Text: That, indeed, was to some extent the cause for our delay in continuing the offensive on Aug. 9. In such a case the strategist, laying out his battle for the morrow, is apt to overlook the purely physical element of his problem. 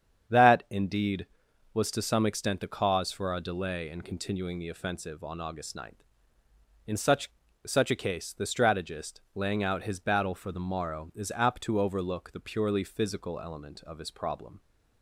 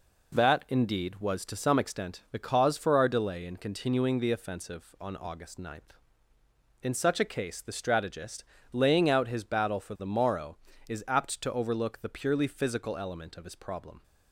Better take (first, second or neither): second